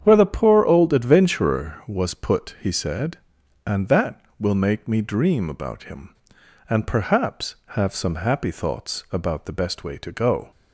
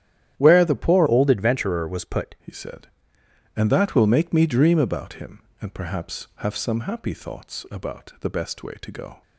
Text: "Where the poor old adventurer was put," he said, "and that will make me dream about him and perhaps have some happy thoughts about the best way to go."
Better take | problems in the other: first | starts louder than the rest; strong; until 1.3 s; 10.5 dB; strong in the first // changes voice from "old" to "put"; from 1.0 to 2.3 s; 1.3 s long

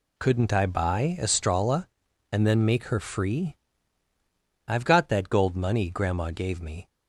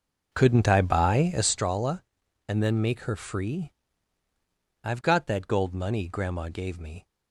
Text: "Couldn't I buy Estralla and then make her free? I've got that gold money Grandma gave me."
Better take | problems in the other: first | starts louder than the rest; noticeable; until 1.5 s; 5.5 dB

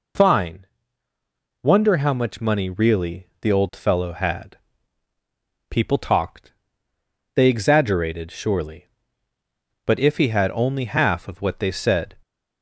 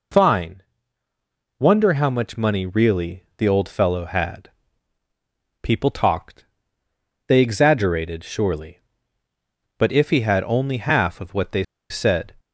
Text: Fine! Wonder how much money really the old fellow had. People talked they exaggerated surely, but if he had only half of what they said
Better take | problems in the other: first | pauses between "really" and "the"; slight; at 3.2 s; 0.16 s long; slight in the first // pauses between "talked" and "they"; noticeable; at 6.4 s; 0.84 s long; noticeable in the first // pauses between "they" and "said"; slight; at 11.6 s; 0.25 s long

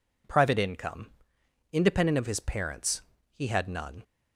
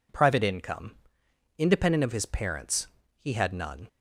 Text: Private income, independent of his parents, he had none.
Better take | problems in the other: neither | none

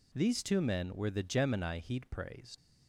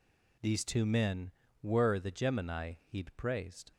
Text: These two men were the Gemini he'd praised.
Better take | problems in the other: second | leaves "praised" unfinished; at 2.5 s; 95 ms

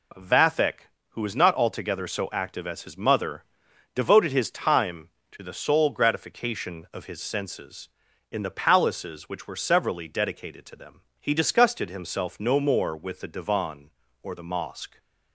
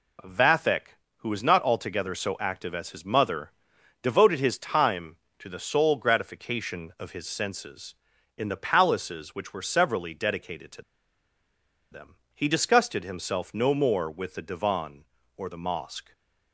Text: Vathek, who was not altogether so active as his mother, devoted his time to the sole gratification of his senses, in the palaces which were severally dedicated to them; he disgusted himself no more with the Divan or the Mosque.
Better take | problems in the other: first | pauses between "to" and "them"; at 10.8 s; 1.0 s long // stays silent after the last word; slight; from 16.0 s on; 0.5 s long

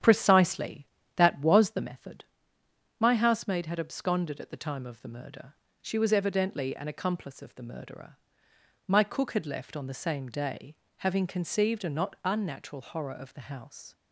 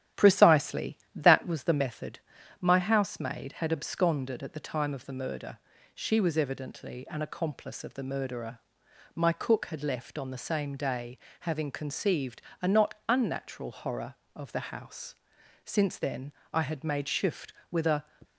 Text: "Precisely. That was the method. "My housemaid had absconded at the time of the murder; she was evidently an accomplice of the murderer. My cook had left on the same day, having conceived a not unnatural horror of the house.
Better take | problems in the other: first | starts louder than the rest; strong; until 1.3 s; 11.5 dB; strong in the first // pauses between "conceived" and "a"; slight; at 12.4 s; 0.20 s long // pauses between "not" and "unnatural"; slight; at 12.9 s; 0.16 s long // goes on to say "Since then I had made shift with a"; strong; from 15.6 s on; 2.3 s long

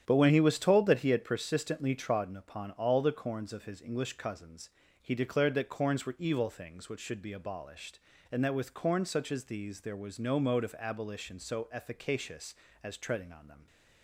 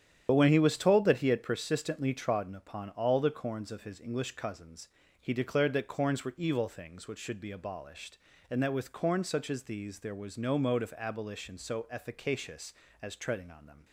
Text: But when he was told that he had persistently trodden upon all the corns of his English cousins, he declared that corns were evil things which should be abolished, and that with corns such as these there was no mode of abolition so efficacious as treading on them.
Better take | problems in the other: first | loses the start of "But"; at 0.2 s; 45 ms // starts louder than the rest; strong; until 1.3 s; 10 dB; strong in the first

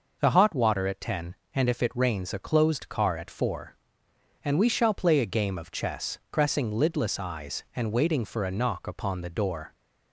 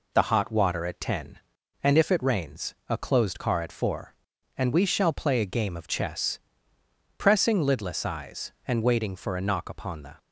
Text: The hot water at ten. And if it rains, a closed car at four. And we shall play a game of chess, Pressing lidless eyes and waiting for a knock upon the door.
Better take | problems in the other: first | stops before "door"; at 10.1 s

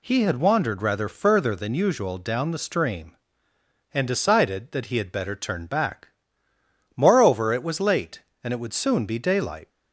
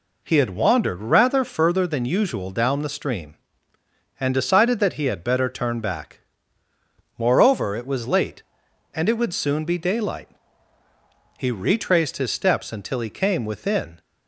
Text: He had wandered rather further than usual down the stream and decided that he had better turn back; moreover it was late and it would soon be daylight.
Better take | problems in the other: first | goes on to say "He retraced his steps until he came within"; strong; from 11.3 s on; 2.6 s long

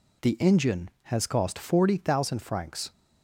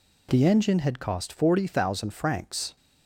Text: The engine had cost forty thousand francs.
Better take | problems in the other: second | says "has" for "had"; at 1.0 s

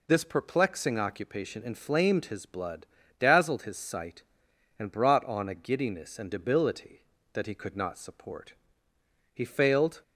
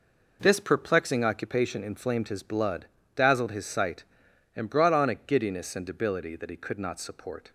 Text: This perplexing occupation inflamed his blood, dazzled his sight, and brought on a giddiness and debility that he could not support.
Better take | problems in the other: second | goes on to say "He failed"; noticeable; from 9.3 s on; 0.68 s long

